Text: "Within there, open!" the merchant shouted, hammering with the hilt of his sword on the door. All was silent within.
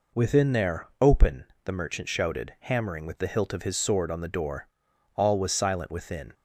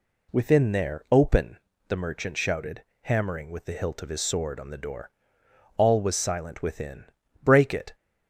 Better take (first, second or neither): first